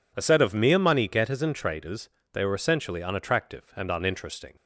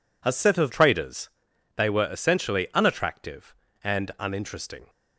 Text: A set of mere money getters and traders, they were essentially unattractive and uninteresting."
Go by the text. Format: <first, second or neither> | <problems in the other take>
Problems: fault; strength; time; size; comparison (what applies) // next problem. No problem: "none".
first | skips "mere money getters and"; at 0.7 s